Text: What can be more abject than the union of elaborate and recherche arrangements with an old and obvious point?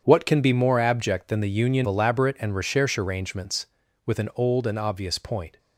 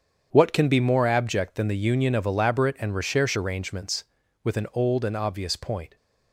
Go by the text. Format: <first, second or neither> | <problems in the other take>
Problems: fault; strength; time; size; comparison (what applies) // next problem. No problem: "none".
second | starts louder than the rest; strong; until 1.0 s; 7.5 dB; strong in the second // skips "of"; at 1.8 s